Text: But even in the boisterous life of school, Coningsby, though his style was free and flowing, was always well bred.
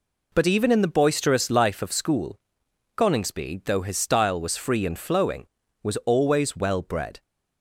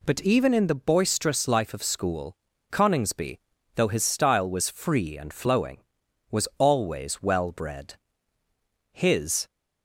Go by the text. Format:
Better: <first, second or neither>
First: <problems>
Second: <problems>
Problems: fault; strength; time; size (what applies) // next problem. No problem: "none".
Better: first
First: none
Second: goes on to say "His"; from 8.9 s on; 0.54 s long